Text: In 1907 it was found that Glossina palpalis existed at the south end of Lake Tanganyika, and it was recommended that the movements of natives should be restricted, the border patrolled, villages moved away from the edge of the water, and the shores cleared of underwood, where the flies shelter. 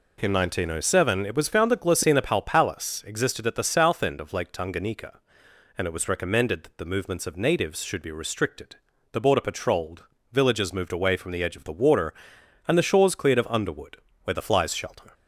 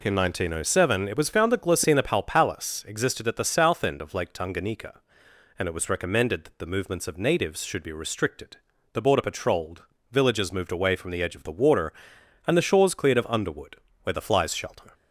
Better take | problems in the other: neither | none

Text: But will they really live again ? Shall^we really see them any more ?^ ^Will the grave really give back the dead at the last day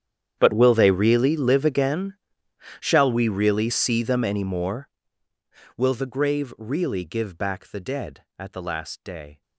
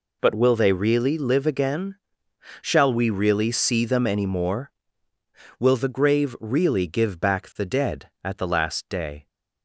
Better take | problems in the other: second | gets quieter; strong; throughout; 22.5 dB

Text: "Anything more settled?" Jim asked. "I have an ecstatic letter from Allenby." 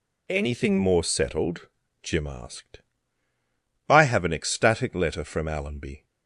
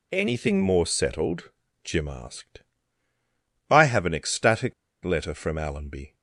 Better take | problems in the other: first | pauses between "ecstatic" and "letter"; slight; at 4.7 s; 0.31 s long

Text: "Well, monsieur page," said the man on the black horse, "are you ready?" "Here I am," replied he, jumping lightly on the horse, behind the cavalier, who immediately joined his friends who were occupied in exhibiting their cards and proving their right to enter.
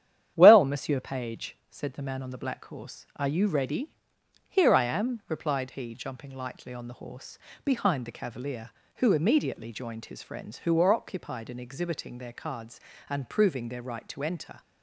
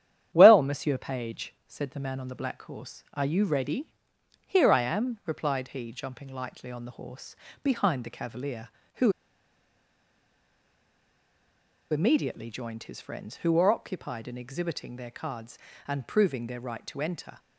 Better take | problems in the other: first | starts louder than the rest; strong; until 1.3 s; 10 dB; strong in the first // pauses between "who" and "immediately"; strong; at 9.1 s; 2.7 s long

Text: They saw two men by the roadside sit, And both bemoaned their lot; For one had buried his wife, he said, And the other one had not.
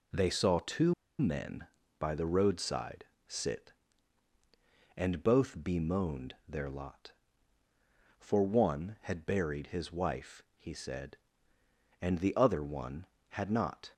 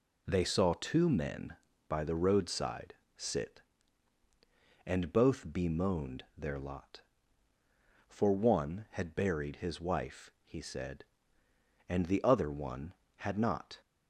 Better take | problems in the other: second | pauses between "two" and "men"; slight; at 0.9 s; 0.25 s long // pauses between "roadside" and "sit"; slight; at 3.0 s; 0.22 s long; slight in the second

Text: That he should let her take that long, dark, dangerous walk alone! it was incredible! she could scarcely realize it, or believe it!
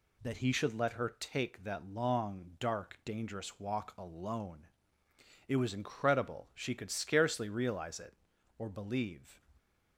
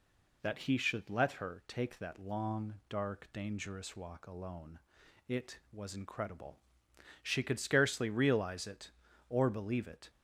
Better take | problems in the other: second | stops before "it"; at 9.5 s

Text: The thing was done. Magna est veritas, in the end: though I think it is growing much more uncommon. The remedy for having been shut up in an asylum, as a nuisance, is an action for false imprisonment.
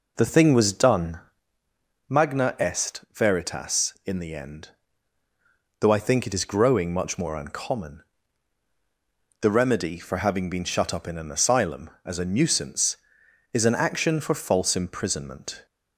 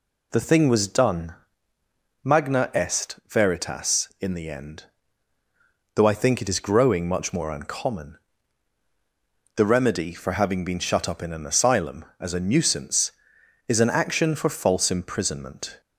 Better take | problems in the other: second | starts louder than the rest; noticeable; until 1.5 s; 4.5 dB

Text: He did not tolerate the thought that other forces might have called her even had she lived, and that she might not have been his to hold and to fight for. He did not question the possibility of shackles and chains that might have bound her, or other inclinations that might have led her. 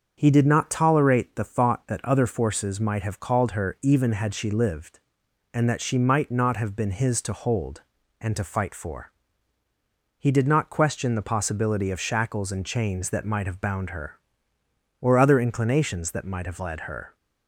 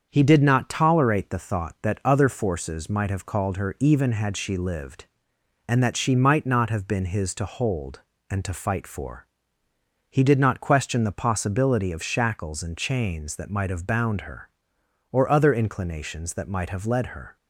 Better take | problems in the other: neither | starts louder than the rest; the same in both

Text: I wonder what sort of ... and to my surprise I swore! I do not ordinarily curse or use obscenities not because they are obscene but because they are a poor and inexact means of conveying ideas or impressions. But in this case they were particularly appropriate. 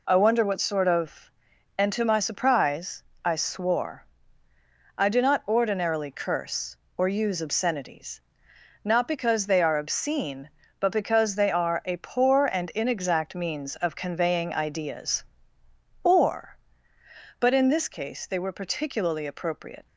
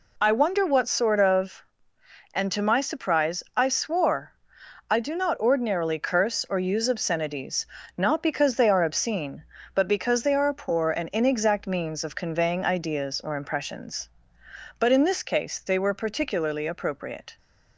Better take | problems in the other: second | pauses between "surprise" and "I"; slight; at 3.0 s; 0.20 s long // pauses between "obscenities" and "not"; noticeable; at 8.2 s; 0.64 s long; slight in the second // skips "impressions"; at 16.9 s

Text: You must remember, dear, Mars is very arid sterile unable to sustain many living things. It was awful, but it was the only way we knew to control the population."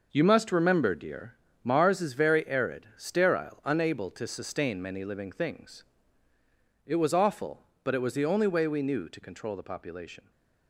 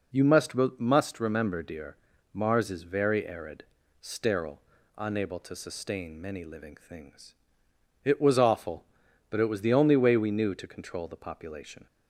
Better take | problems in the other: first | says "must" twice; at 0.5 s // pauses between "arid" and "sterile"; at 3.6 s; 0.38 s long // pauses between "sterile" and "unable"; at 4.5 s; 0.38 s long

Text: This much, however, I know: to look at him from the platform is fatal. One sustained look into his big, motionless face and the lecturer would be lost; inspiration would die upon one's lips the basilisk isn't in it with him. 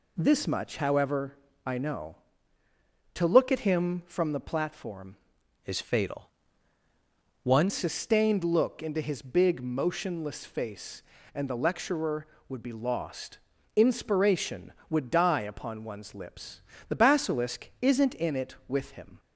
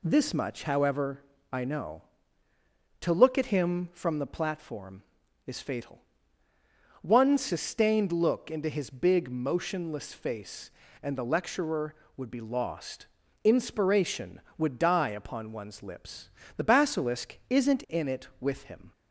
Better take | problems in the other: second | changes voice from "is" to "One"; from 5.6 to 7.6 s; 2.0 s long // pauses between "lips" and "the"; slight; at 16.6 s; 0.28 s long; slight in the second

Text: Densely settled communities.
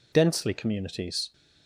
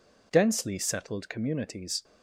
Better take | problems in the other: second | skips "settled"; at 0.5 s

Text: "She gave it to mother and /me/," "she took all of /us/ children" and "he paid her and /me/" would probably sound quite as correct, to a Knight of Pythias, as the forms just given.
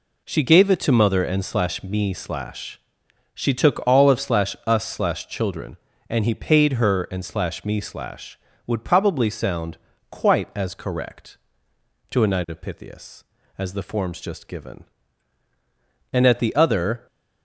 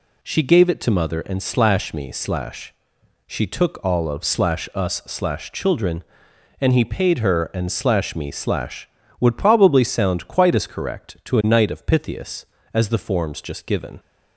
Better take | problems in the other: second | pauses between "sound" and "quite"; slight; at 9.7 s; 0.32 s long // goes on to say "And at the other"; noticeable; from 16.1 s on; 0.94 s long

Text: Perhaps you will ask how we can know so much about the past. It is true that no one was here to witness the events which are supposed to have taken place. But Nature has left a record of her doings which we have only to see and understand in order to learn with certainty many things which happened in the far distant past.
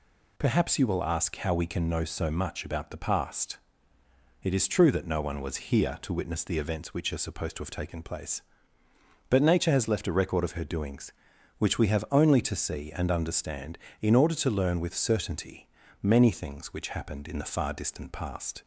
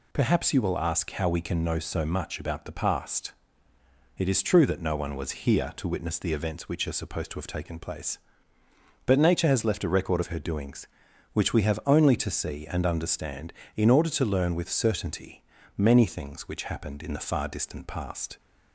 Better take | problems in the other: neither | pauses between "certainty" and "many"; slight; the same in both

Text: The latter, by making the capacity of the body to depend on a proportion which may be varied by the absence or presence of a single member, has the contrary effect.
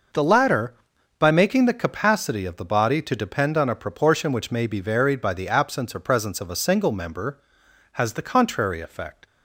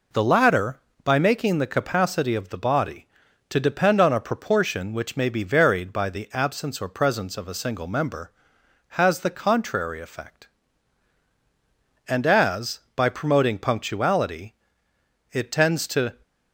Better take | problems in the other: first | goes on to say "And as by promoting punctuality it tends to"; strong; from 12.0 s on; 4.1 s long

